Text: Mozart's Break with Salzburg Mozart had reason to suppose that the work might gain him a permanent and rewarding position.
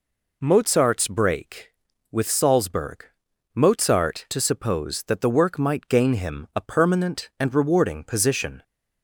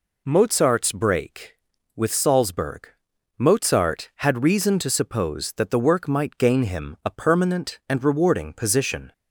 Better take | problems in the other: second | pauses between "Salzburg" and "Mozart"; noticeable; at 3.0 s; 0.50 s long; noticeable in the second // skips "had reason"; at 4.2 s

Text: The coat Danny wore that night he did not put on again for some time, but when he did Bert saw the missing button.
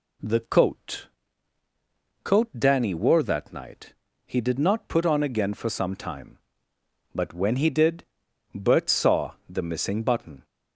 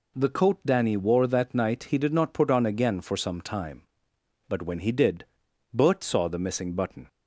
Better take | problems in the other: second | says "coat" twice; at 2.2 s // pauses between "night" and "he"; slight; at 3.9 s; 0.32 s long // pauses between "did" and "Bert"; noticeable; at 8.0 s; 0.50 s long; noticeable in the second // pauses between "saw" and "the"; slight; at 9.3 s; 0.16 s long

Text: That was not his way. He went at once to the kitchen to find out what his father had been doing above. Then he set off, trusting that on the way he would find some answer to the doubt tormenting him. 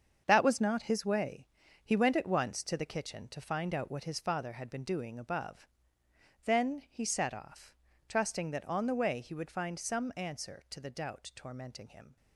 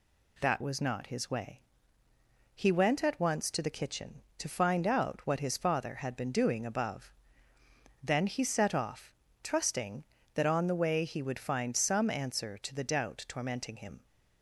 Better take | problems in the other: second | gets quieter; strong; throughout; 9.5 dB

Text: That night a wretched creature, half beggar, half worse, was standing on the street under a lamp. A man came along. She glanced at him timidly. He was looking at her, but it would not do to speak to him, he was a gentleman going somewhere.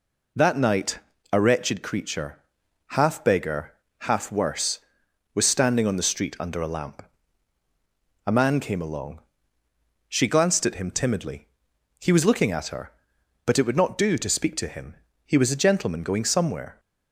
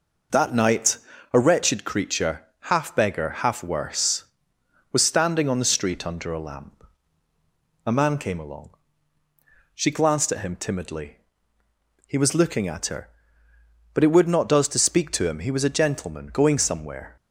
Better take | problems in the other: first | pauses between "night" and "a"; slight; at 0.9 s; 0.34 s long; slight in the first // says "does" for "do"; at 14.4 s

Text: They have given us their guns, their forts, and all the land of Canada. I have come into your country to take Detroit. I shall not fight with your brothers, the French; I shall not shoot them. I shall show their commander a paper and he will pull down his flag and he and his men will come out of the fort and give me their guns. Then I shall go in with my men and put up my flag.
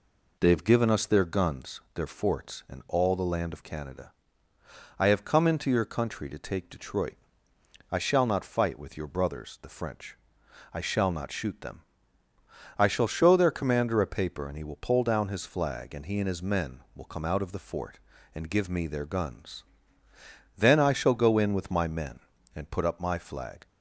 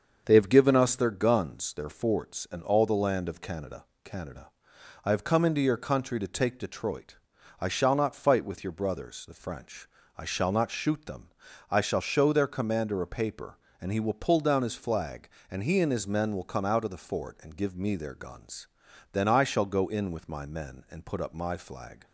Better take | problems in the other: first | starts louder than the rest; until 1.2 s; 6.5 dB // says "Canada" twice; at 4.0 s

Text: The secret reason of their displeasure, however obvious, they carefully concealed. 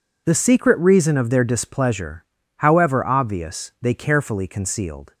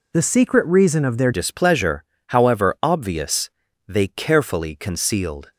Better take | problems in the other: first | changes voice at "displeasure"; from 1.3 s on; 4.2 s long

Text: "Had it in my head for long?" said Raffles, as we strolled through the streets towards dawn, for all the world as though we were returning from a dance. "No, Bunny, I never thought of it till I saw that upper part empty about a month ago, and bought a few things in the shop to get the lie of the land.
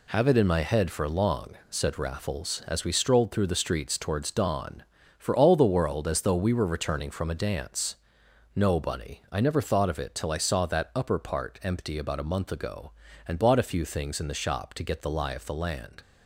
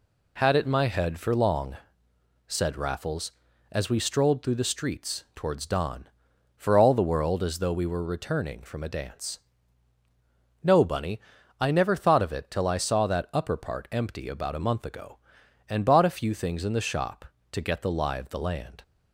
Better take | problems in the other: second | says "Have" for "Had"; at 0.0 s

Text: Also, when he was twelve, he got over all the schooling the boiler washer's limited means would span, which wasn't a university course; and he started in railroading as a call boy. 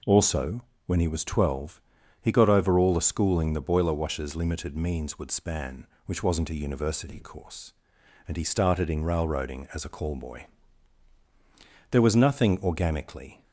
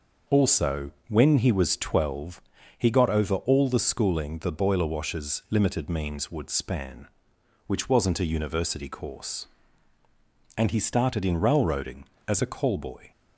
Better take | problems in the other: second | goes on to say "There was nothing organically"; from 11.9 s on; 1.5 s long

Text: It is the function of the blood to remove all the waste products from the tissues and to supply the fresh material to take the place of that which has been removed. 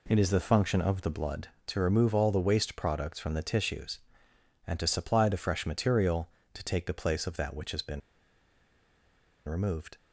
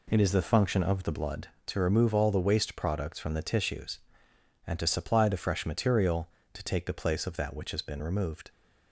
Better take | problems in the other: second | pauses between "been" and "removed"; strong; at 8.0 s; 1.4 s long

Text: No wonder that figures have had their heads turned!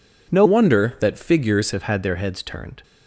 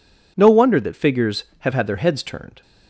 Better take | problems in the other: second | changes voice from "wonder" to "figures"; from 0.4 to 1.7 s; 1.3 s long

